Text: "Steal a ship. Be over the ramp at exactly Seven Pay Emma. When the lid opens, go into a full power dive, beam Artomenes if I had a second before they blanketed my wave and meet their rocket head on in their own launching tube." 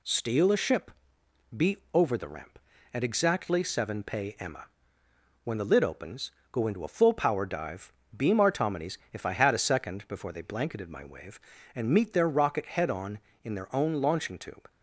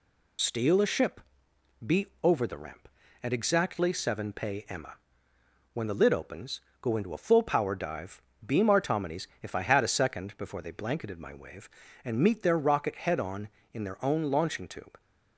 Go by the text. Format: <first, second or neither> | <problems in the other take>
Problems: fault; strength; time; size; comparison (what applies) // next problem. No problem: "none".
first | loses the start of "Steal"; at 0.3 s; 55 ms // pauses between "Be" and "over"; slight; at 2.0 s; 0.16 s long; slight in the first // pauses between "Artomenes" and "if"; slight; at 9.2 s; 0.16 s long; slight in the first